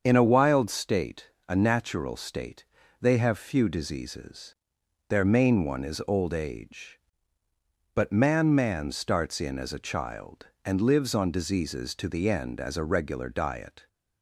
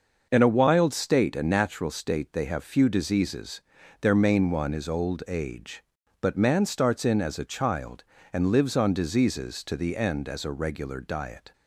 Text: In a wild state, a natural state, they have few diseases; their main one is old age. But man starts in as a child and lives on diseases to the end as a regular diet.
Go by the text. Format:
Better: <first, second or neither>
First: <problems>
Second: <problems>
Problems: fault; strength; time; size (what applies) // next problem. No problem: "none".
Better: second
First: starts louder than the rest; until 1.0 s; 7 dB // says "man" twice; at 8.5 s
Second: starts louder than the rest; noticeable; until 1.3 s; 6 dB